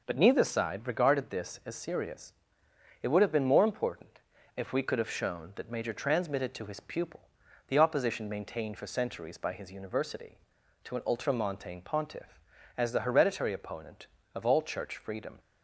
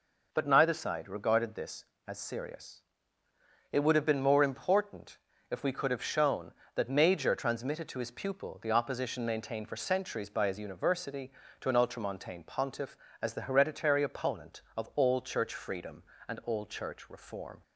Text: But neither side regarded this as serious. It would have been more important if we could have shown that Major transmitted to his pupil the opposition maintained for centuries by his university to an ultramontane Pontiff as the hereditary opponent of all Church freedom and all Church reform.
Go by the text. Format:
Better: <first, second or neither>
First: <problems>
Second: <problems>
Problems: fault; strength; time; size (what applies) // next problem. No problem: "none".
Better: second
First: pauses between "important" and "if"; at 4.1 s; 0.38 s long // pauses between "pupil" and "the"; noticeable; at 7.2 s; 0.46 s long // stops before "and all Church reform"; at 15.3 s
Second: pauses between "important" and "if"; slight; at 5.1 s; 0.32 s long